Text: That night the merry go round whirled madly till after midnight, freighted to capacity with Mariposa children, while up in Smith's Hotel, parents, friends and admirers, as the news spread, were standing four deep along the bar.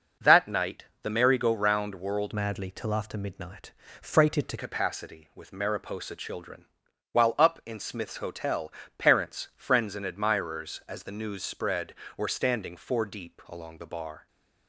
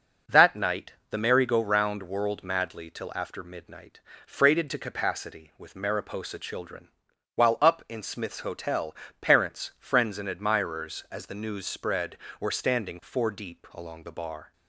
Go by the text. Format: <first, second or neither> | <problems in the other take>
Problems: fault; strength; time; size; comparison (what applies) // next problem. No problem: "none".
second | starts louder than the rest; noticeable; until 1.3 s; 6 dB // pauses between "night" and "the"; slight; at 0.8 s; 0.18 s long; slight in the second // changes voice from "madly" to "to"; from 2.3 to 4.5 s; 2.2 s long